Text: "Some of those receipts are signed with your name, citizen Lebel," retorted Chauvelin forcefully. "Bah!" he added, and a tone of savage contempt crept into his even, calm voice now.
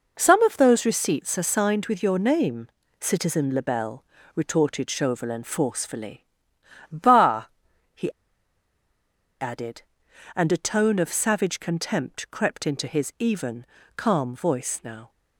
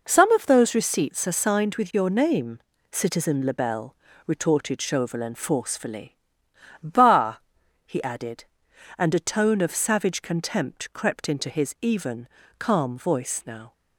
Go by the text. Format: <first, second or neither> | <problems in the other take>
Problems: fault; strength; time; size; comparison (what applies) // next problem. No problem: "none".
second | pauses between "he" and "added"; strong; at 8.0 s; 1.3 s long